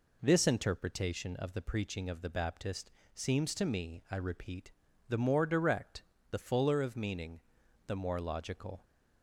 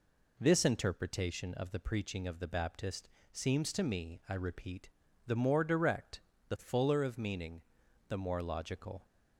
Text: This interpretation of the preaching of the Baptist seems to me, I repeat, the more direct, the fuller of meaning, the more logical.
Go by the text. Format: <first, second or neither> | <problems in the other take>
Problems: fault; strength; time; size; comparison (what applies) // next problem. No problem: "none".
neither | pauses between "Baptist" and "seems"; slight; the same in both